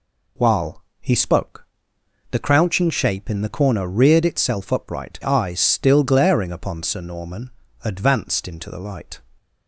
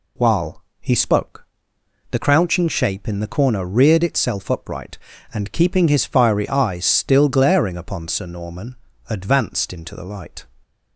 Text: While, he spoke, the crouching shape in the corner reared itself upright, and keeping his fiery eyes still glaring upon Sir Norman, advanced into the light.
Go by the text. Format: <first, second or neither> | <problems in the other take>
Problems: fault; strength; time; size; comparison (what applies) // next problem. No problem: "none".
second | skips "and keeping his fiery"; at 5.2 s